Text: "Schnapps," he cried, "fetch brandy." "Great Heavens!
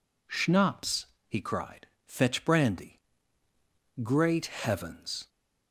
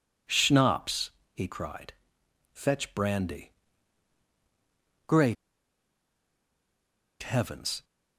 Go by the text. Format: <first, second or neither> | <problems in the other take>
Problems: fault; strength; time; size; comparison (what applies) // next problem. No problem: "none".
first | pauses between "Great" and "Heavens"; strong; at 5.3 s; 1.8 s long